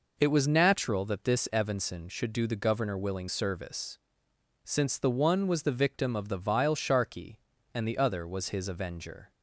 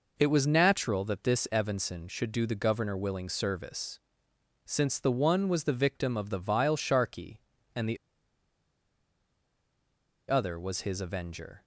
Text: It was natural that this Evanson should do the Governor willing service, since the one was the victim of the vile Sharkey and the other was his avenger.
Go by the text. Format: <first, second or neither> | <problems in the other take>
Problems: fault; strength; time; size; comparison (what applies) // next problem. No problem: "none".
first | pauses between "the" and "other"; strong; at 7.9 s; 2.3 s long